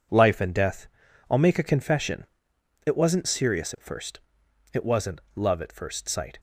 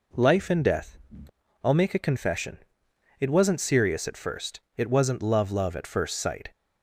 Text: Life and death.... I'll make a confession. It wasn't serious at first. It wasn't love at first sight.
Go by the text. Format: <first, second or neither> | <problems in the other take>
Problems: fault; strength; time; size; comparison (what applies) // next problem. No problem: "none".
first | says "love" twice; at 5.4 s